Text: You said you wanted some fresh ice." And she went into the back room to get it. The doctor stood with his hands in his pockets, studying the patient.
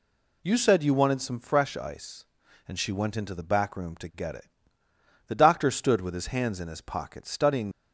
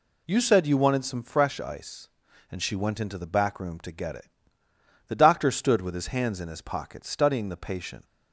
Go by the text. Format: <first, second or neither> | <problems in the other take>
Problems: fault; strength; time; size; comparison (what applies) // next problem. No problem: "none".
second | stops before "the patient"; at 7.7 s